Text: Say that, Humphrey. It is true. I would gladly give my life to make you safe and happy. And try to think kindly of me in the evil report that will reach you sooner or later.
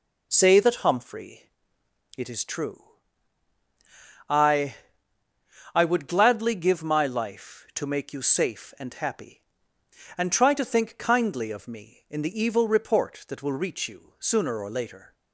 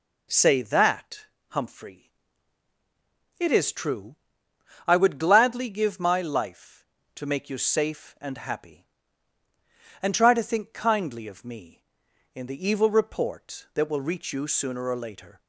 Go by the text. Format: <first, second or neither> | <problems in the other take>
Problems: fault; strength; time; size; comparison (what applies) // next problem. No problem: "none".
second | says "I" twice; at 5.7 s